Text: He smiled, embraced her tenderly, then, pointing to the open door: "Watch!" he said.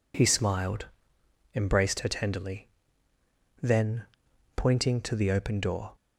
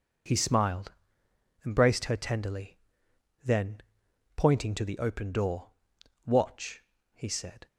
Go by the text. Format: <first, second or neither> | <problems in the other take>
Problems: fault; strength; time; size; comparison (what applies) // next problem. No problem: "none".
second | stops before "Watch he said"; at 5.9 s